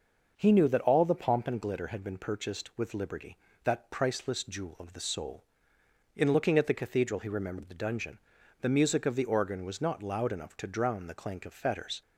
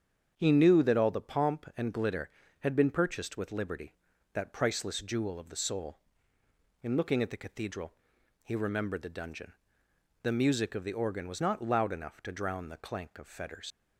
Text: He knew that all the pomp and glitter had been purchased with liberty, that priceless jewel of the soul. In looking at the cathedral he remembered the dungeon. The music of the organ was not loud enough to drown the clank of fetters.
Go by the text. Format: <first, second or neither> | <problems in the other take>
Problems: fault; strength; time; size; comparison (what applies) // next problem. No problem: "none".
first | starts louder than the rest; strong; until 1.3 s; 7.5 dB; noticeable in the first // pauses between "cathedral" and "he"; noticeable; at 7.9 s; 0.50 s long // leaves "fetters" unfinished; at 13.7 s; 95 ms